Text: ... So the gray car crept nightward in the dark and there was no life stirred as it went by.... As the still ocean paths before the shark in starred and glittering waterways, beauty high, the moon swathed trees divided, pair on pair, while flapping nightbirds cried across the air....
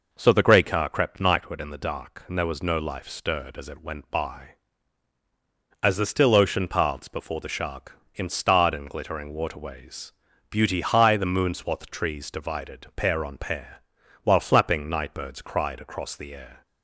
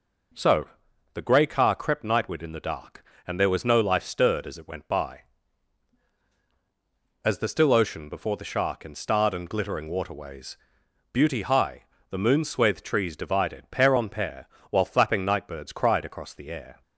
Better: first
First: none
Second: pauses between "So" and "the"; at 0.6 s; 0.44 s long // skips "paths"; at 8.0 s

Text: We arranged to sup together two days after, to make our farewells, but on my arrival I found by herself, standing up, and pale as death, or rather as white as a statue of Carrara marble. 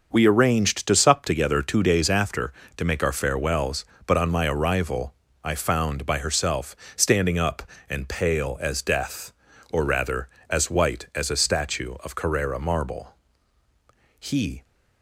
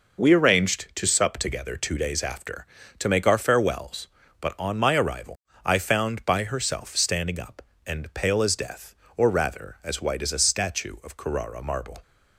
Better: second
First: starts louder than the rest; until 1.1 s; 6 dB // pauses between "arrival" and "I"; slight; at 5.1 s; 0.28 s long // goes on to say "He"; slight; from 14.1 s on; 0.44 s long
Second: pauses between "arrival" and "I"; slight; at 5.3 s; 0.28 s long

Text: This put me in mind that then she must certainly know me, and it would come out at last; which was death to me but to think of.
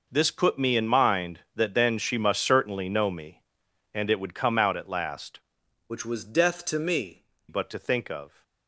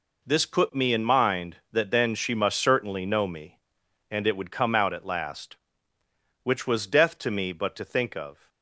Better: second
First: changes voice from "which" to "me"; from 5.8 to 7.2 s; 1.4 s long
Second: none

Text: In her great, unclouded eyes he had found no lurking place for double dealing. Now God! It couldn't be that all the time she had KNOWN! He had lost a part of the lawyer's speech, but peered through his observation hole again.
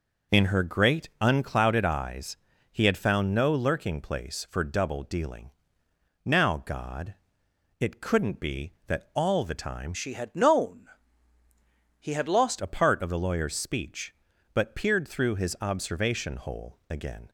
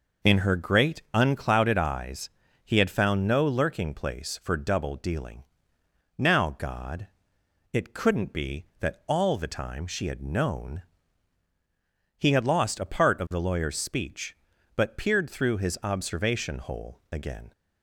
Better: second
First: pauses between "eyes" and "he"; slight; at 2.3 s; 0.34 s long // changes voice from "she" to "lost"; from 9.9 to 12.5 s; 2.6 s long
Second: pauses between "eyes" and "he"; slight; at 2.2 s; 0.34 s long

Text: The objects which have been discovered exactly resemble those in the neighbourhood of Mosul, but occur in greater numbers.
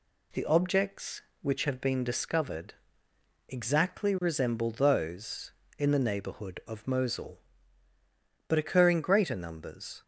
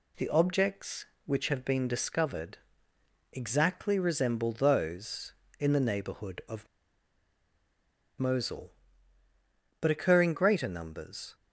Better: first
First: pauses between "discovered" and "exactly"; noticeable; at 2.7 s; 0.78 s long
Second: pauses between "discovered" and "exactly"; noticeable; at 2.5 s; 0.78 s long // pauses between "of" and "Mosul"; strong; at 6.6 s; 1.5 s long

